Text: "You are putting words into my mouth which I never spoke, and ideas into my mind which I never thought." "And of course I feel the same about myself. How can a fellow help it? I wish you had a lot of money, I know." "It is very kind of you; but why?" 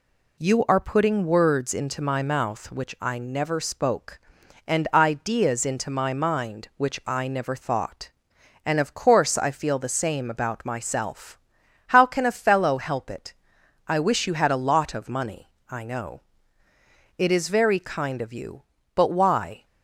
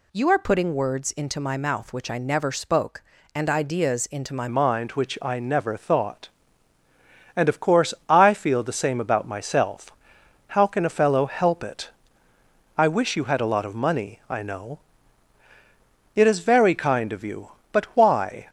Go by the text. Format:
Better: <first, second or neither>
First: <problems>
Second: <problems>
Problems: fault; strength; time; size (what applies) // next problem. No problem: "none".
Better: first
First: none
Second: changes voice at "mind"; from 4.4 s on; 14.0 s long // pauses between "course" and "I"; slight; at 7.9 s; 0.16 s long